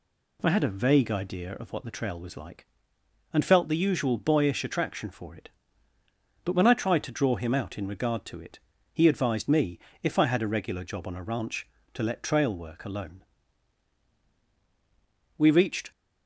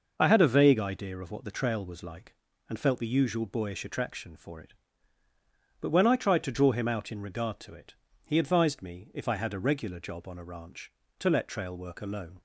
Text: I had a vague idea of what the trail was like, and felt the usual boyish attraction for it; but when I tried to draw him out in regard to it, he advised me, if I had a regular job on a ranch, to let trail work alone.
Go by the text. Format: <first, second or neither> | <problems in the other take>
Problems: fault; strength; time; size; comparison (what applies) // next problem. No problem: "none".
second | goes on to say "We reached"; from 15.3 s on; 0.54 s long